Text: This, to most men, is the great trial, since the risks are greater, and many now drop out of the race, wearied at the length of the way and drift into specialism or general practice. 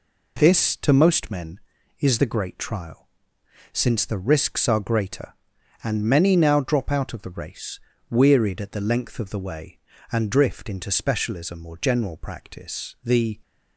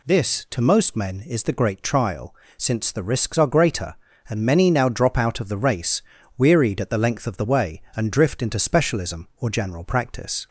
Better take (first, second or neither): second